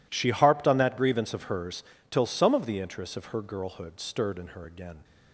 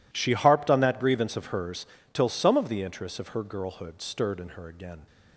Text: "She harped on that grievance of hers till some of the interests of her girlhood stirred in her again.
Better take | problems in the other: neither | pauses between "hers" and "till"; slight; the same in both

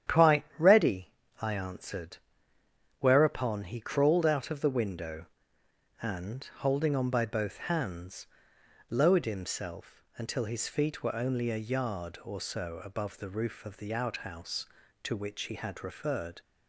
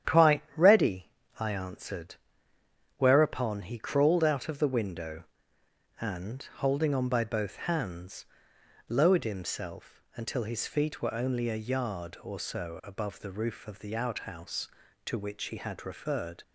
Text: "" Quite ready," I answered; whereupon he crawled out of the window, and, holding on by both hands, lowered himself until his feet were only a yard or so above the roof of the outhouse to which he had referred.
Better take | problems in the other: neither | starts louder than the rest; strong; the same in both

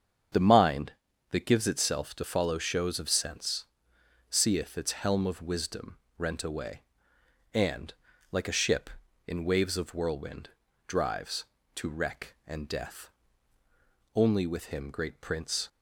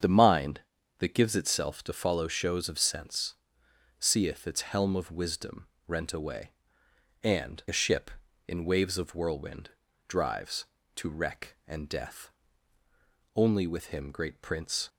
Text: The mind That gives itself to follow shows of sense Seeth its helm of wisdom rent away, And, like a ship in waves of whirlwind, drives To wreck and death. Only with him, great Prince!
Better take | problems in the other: first | starts louder than the rest; strong; until 1.3 s; 7.5 dB; strong in the first // pauses between "sense" and "Seeth"; noticeable; at 3.3 s; 0.64 s long; noticeable in the first // pauses between "wisdom" and "rent"; slight; at 5.6 s; 0.18 s long; slight in the first // skips "like"; at 7.6 s

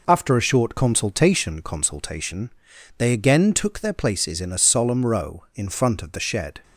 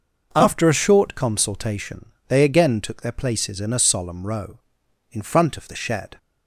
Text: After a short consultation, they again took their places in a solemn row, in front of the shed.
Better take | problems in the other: second | says "consultation" twice; at 1.6 s

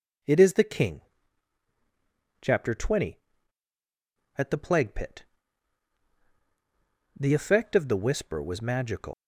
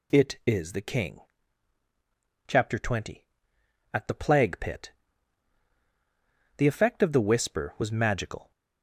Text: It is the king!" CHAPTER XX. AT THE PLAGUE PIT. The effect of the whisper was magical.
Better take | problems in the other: second | leaves "magical" unfinished; at 9.1 s; 110 ms

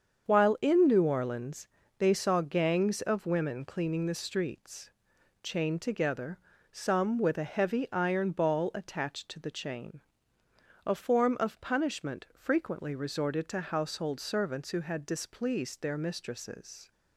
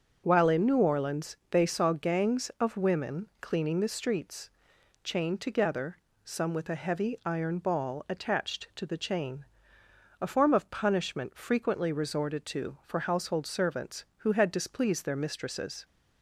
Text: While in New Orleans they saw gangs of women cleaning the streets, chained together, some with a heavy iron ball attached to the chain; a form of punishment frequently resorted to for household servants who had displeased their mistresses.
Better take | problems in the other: second | starts louder than the rest; strong; until 1.3 s; 7 dB; also in the second // pauses between "Orleans" and "they"; slight; at 1.6 s; 0.30 s long // skips "for"; at 13.6 s

